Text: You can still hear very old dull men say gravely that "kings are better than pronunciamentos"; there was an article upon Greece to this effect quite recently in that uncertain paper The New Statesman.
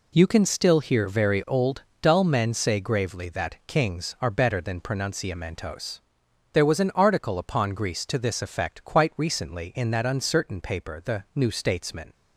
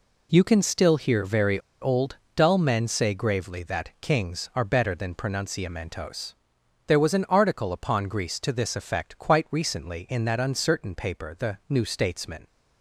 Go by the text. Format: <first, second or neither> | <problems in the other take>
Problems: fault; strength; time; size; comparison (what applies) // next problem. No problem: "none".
first | pauses between "very" and "old"; slight; at 1.5 s; 0.22 s long // pauses between "old" and "dull"; slight; at 2.1 s; 0.18 s long; slight in the first